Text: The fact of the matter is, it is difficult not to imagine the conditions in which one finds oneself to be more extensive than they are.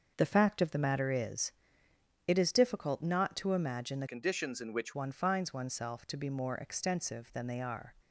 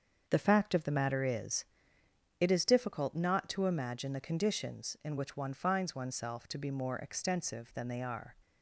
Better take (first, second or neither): second